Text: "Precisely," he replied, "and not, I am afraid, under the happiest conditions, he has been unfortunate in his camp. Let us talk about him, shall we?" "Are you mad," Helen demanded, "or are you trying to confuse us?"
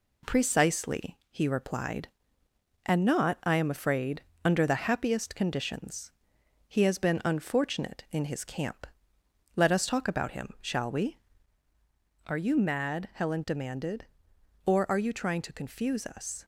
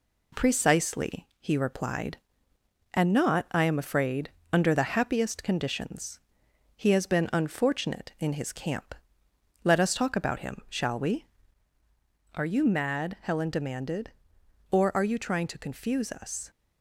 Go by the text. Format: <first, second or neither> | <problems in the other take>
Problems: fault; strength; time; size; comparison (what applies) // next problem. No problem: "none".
neither | none